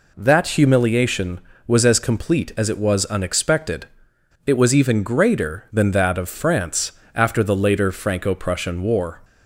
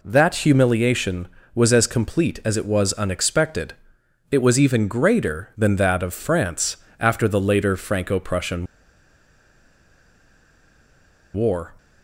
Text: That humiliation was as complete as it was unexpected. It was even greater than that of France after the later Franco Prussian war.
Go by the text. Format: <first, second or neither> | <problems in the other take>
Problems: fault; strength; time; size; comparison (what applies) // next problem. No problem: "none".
first | pauses between "France" and "after"; slight; at 6.7 s; 0.22 s long; slight in the first // pauses between "Prussian" and "war"; strong; at 8.6 s; 2.6 s long